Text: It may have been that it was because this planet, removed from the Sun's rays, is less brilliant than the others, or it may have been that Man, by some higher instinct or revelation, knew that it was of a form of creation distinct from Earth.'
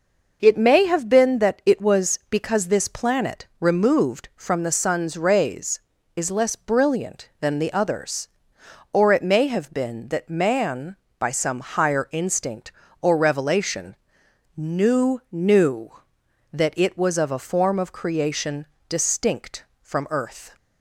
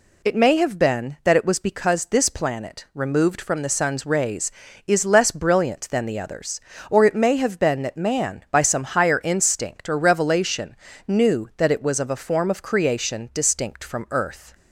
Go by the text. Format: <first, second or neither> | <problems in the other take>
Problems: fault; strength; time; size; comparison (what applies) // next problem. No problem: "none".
second | says "knew" twice; at 15.3 s // pauses between "creation" and "distinct"; slight; at 18.6 s; 0.24 s long